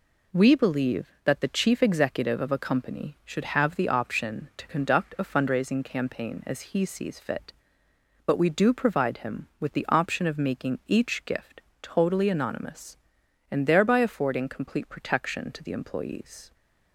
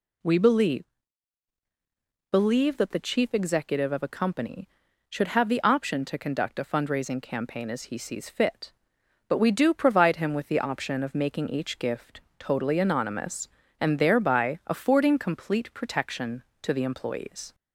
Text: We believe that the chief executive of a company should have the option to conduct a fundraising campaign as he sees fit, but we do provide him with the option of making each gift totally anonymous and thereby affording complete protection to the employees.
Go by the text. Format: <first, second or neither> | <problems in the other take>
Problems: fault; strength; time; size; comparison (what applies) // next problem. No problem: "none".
first | says "believe" twice; at 2.3 s // pauses between "gift" and "totally"; slight; at 12.2 s; 0.18 s long; slight in the first